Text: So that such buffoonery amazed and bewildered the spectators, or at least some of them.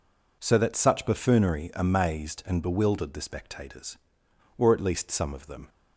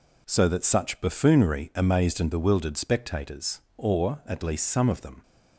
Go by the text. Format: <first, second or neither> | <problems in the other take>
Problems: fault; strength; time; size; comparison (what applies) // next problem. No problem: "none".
first | skips "the"; at 2.7 s